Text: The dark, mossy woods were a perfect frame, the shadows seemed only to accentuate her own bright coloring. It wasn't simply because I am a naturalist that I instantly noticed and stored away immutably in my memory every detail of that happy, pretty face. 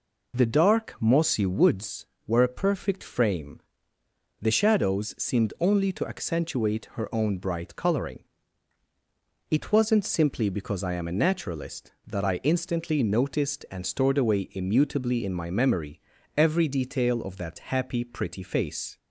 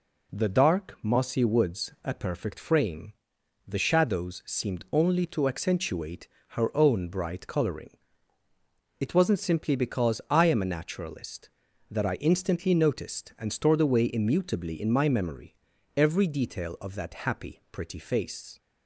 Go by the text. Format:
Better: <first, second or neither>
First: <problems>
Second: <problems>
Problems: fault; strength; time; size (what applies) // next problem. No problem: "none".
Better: first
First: pauses between "memory" and "every"; slight; at 16.0 s; 0.36 s long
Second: skips "were"; at 1.9 s // pauses between "accentuate" and "her"; slight; at 6.2 s; 0.22 s long // pauses between "memory" and "every"; at 15.5 s; 0.40 s long